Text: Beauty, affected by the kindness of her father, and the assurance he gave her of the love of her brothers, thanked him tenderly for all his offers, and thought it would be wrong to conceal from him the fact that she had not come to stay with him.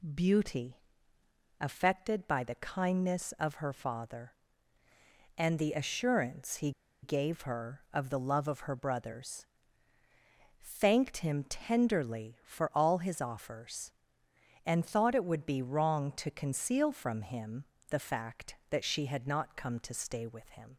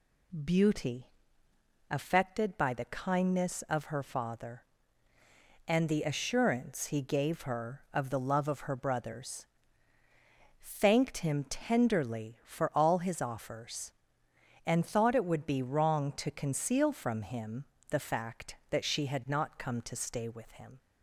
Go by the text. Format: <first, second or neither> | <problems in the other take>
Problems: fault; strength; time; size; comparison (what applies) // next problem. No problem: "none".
second | pauses between "he" and "gave"; slight; at 6.7 s; 0.32 s long // pauses between "him" and "the"; slight; at 17.6 s; 0.24 s long; slight in the second